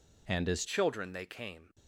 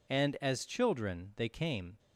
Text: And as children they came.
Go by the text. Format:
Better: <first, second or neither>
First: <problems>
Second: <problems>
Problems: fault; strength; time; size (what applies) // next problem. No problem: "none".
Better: second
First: changes voice at "children"; from 0.6 s on; 1.1 s long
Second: none